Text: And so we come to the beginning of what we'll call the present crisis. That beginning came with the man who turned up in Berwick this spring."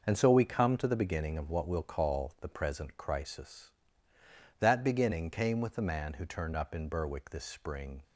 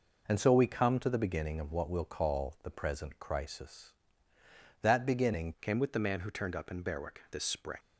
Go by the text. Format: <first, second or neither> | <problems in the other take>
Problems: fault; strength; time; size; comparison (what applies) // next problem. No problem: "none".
first | changes voice at "came"; from 5.6 s on; 2.1 s long